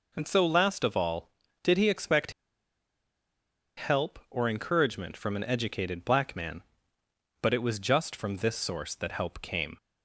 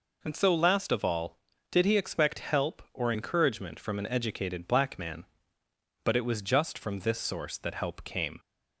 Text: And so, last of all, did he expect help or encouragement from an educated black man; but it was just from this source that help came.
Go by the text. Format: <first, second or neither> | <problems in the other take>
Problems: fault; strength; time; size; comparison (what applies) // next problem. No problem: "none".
second | pauses between "expect" and "help"; strong; at 2.3 s; 1.4 s long